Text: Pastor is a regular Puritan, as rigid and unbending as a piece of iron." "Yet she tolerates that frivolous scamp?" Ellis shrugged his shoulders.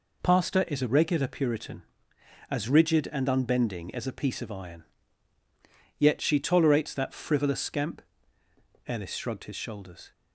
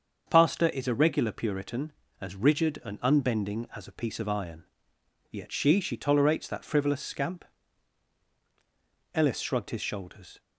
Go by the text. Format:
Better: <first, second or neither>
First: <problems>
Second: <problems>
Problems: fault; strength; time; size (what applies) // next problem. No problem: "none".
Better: first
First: none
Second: starts louder than the rest; until 1.2 s; 6.5 dB // says "she" twice; at 5.7 s